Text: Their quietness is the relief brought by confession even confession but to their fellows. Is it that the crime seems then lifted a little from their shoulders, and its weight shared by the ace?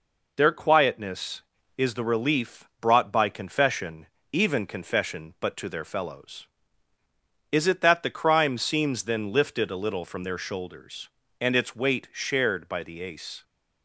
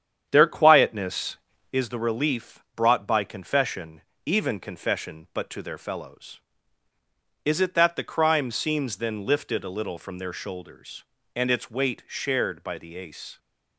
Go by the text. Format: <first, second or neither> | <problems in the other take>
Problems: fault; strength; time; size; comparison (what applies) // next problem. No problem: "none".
first | starts louder than the rest; strong; until 1.8 s; 8.5 dB // pauses between "confession" and "even"; slight; at 4.0 s; 0.26 s long; slight in the first